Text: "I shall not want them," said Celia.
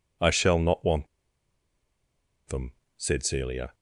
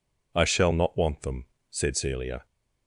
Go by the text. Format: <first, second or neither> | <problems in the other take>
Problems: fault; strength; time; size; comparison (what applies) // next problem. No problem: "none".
second | pauses between "want" and "them"; strong; at 1.0 s; 1.4 s long